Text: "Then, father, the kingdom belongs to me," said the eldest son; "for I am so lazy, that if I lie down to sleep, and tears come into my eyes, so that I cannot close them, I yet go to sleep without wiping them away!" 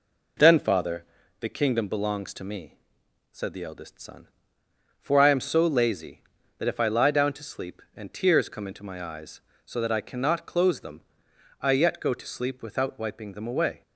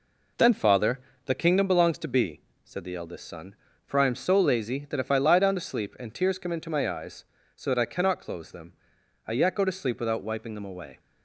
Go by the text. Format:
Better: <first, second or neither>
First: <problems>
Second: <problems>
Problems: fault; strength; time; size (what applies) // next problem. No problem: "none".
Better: first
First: none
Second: says "be" for "me"; at 2.0 s